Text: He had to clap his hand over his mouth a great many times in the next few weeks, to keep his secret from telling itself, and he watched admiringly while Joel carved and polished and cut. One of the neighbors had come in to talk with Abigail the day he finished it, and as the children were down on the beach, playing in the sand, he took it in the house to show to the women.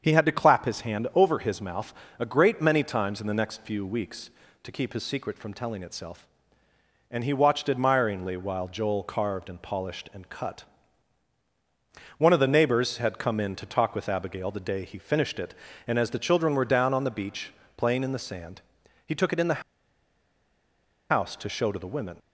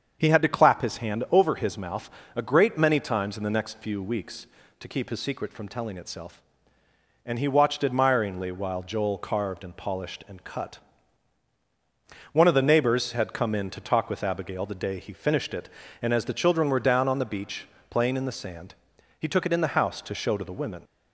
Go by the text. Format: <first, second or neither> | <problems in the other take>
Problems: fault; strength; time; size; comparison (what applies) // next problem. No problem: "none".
second | starts louder than the rest; strong; until 1.0 s; 7 dB; strong in the second // pauses between "mouth" and "a"; slight; at 1.9 s; 0.26 s long; slight in the second // pauses between "the" and "house"; strong; at 19.6 s; 1.5 s long